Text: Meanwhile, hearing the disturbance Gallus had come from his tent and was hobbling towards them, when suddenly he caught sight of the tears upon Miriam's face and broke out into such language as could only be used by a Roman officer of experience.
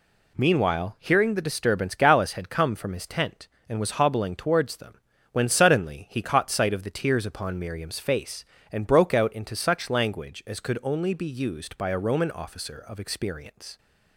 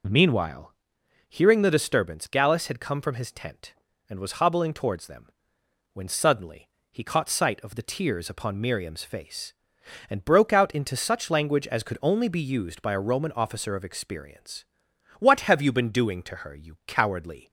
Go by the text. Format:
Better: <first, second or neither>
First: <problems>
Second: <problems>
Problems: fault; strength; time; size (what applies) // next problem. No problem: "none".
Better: first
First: none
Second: pauses between "suddenly" and "he"; slight; at 6.6 s; 0.24 s long // goes on to say "What have you been doing to her you cowardly"; strong; from 15.1 s on; 2.3 s long